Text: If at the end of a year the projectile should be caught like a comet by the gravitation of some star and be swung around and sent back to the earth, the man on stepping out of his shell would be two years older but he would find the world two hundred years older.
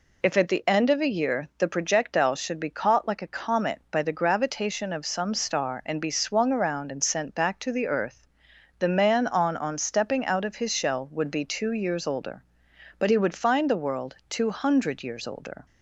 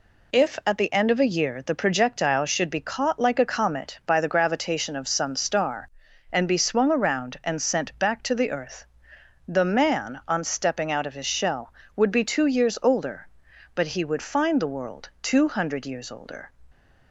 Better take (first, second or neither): second